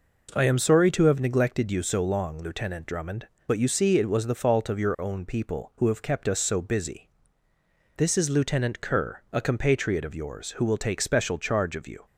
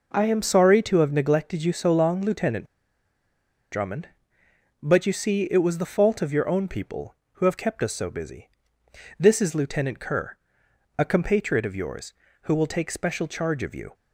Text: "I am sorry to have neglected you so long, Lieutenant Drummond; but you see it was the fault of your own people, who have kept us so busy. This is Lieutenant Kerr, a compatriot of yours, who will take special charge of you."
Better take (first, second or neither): first